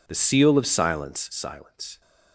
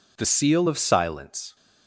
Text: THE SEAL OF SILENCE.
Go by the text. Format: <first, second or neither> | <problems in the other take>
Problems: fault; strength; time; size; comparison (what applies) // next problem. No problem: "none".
second | says "SILENCE" twice; at 1.3 s